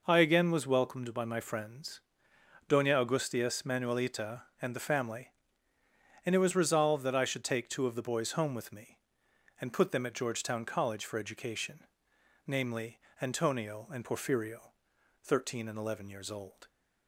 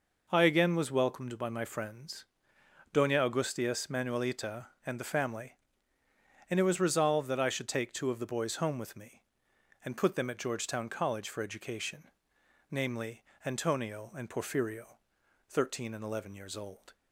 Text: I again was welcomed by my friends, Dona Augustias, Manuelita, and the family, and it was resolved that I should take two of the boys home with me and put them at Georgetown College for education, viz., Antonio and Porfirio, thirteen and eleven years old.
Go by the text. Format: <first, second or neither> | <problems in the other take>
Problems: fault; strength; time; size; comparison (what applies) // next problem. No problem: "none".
neither | none